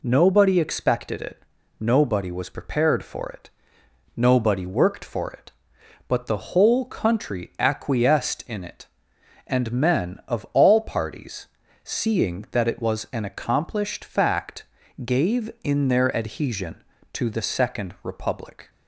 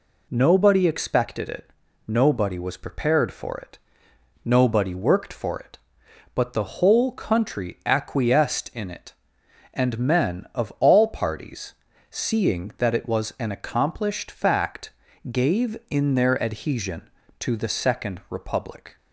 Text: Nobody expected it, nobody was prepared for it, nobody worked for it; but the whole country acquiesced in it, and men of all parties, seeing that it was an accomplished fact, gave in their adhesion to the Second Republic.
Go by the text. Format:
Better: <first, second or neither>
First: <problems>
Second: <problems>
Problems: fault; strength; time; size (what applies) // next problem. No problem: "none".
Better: neither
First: none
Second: none